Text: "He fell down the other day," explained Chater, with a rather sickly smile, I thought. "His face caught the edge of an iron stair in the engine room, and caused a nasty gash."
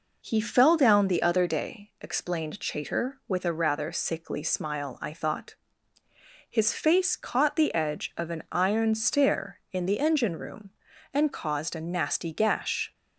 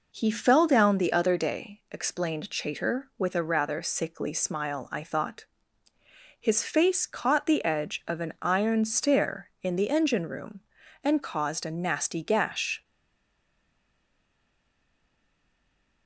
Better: first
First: none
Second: stays silent after the last word; strong; from 12.8 s on; 3.2 s long

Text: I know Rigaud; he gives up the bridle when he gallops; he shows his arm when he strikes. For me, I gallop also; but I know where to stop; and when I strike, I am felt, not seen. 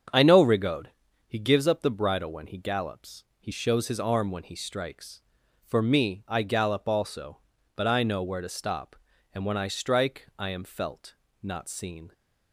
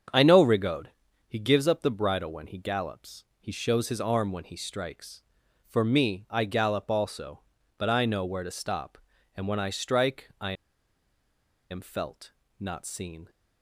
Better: first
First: starts louder than the rest; strong; until 1.5 s; 7.5 dB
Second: starts louder than the rest; strong; until 1.5 s; 7.5 dB // pauses between "I" and "am"; at 10.5 s; 1.1 s long

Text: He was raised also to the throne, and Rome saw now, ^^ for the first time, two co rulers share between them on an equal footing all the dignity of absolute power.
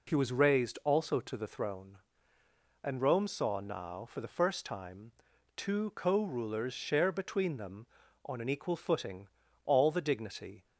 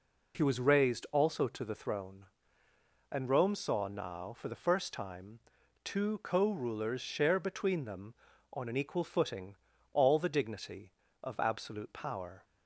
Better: second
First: pauses between "footing" and "all"; at 9.2 s; 0.38 s long // stops before "of absolute power"; at 10.6 s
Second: pauses between "footing" and "all"; at 9.5 s; 0.38 s long

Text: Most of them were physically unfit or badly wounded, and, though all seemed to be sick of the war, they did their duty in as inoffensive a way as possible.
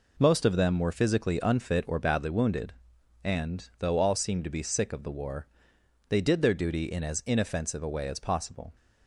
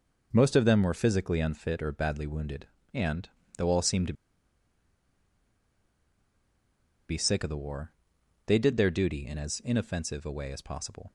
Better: first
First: none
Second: pauses between "to" and "be"; strong; at 4.1 s; 2.9 s long

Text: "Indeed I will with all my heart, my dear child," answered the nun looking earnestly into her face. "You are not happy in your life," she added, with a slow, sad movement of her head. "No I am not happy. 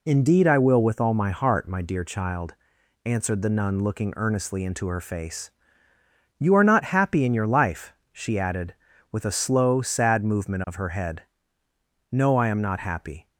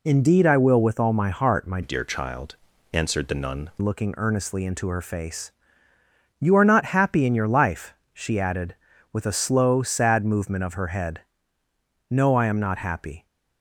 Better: first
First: none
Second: changes voice from "dear" to "nun"; from 1.8 to 3.7 s; 1.9 s long

